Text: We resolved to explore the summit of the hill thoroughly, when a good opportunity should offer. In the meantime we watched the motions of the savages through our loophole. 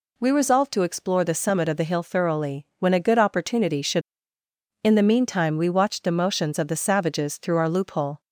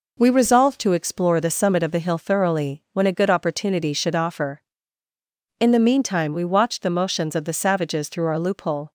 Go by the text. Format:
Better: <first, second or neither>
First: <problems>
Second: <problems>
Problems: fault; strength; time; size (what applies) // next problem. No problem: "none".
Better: second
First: skips "offer"; at 4.4 s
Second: none